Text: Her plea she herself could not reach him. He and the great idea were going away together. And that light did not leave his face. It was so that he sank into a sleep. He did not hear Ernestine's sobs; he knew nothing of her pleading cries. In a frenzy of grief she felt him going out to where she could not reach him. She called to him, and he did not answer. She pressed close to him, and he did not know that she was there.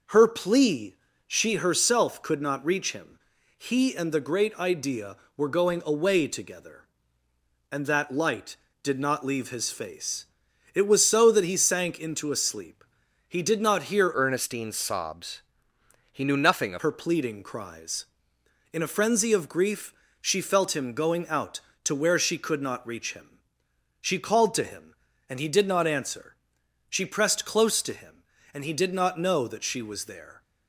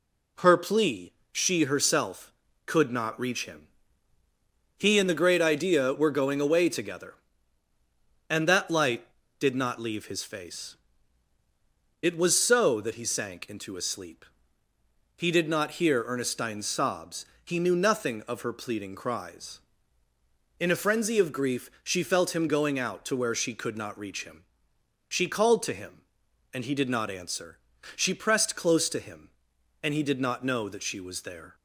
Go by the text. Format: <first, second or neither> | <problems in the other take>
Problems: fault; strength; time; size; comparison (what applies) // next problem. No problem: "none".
second | pauses between "plea" and "she"; slight; at 0.9 s; 0.32 s long; slight in the second // changes voice from "Ernestine's" to "of"; from 14.1 to 16.8 s; 2.7 s long // pauses between "grief" and "she"; slight; at 19.9 s; 0.30 s long